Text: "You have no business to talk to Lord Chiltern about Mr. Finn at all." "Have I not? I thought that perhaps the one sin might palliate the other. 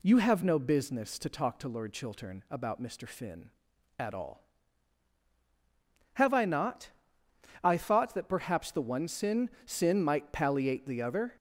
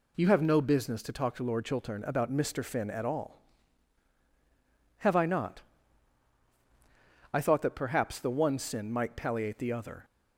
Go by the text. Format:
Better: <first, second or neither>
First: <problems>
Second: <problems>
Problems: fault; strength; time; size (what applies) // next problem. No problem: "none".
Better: second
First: says "sin" twice; at 9.6 s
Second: none